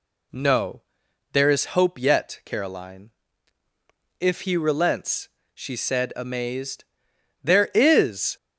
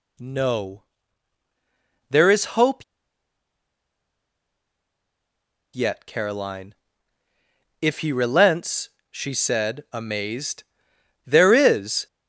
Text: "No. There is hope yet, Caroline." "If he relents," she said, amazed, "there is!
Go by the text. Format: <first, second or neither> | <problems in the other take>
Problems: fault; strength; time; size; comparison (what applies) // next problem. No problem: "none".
first | pauses between "hope" and "yet"; strong; at 2.8 s; 2.9 s long